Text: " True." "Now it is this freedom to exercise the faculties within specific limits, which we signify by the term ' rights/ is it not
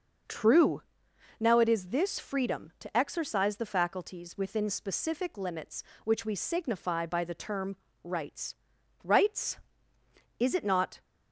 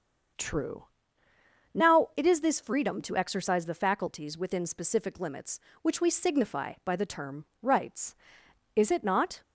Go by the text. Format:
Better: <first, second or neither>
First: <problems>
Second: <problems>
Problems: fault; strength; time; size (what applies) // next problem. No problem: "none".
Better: second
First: starts louder than the rest; until 1.8 s; 6.5 dB // says "rights" twice; at 9.0 s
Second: starts louder than the rest; until 2.2 s; 6.5 dB